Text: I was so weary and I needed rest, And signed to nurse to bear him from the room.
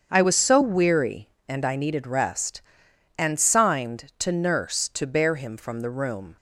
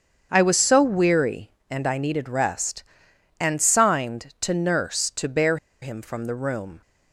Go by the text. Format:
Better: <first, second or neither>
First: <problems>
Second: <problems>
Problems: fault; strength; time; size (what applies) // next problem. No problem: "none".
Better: first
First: starts louder than the rest; strong; until 1.1 s; 7.5 dB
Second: starts louder than the rest; strong; until 1.3 s; 7.5 dB // pauses between "bear" and "him"; slight; at 5.5 s; 0.25 s long